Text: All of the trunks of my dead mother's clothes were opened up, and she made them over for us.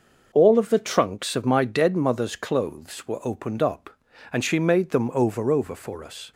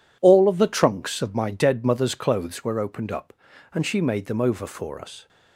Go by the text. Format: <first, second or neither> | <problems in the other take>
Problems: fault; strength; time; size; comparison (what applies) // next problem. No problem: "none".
second | says "over" twice; at 5.4 s